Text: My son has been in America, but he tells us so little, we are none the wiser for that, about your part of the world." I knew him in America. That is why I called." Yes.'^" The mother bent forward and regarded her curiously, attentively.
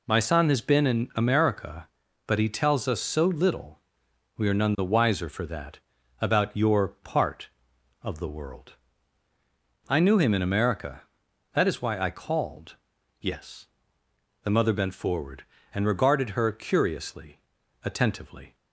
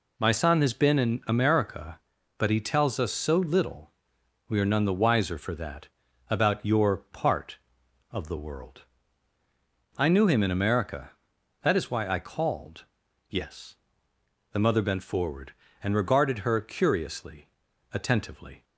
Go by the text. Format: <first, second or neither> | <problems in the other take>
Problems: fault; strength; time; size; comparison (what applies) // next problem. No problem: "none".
neither | none